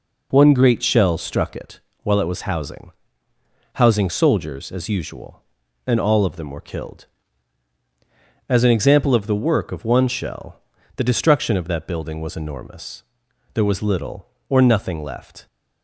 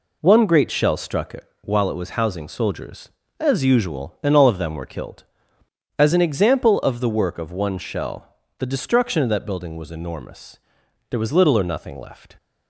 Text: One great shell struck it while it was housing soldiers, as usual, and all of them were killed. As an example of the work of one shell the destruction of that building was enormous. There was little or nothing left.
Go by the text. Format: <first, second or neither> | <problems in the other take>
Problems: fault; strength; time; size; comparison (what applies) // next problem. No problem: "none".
second | pauses between "it" and "while"; slight; at 1.8 s; 0.22 s long; slight in the second // says "housing" twice; at 3.7 s // pauses between "shell" and "the"; slight; at 10.6 s; 0.34 s long; slight in the second